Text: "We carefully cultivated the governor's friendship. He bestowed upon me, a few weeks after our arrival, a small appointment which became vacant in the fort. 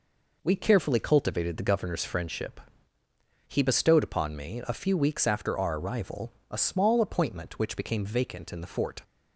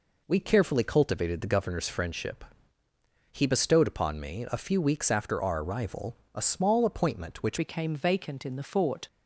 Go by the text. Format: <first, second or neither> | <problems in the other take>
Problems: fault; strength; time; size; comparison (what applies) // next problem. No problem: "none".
first | changes voice at "became"; from 7.5 s on; 1.5 s long